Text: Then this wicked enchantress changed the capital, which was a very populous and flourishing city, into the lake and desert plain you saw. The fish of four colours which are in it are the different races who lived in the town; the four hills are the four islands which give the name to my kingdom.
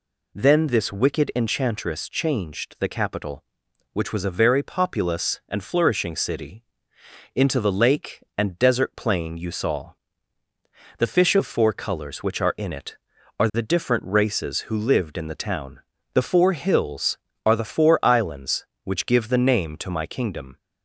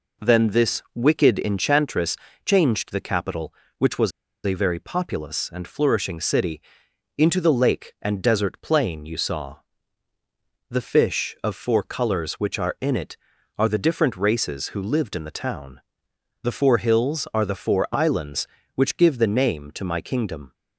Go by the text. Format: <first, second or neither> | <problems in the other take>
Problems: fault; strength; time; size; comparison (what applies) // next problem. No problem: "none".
first | pauses between "enchantress" and "changed"; slight; at 2.1 s; 0.28 s long // pauses between "was" and "a"; slight; at 4.1 s; 0.33 s long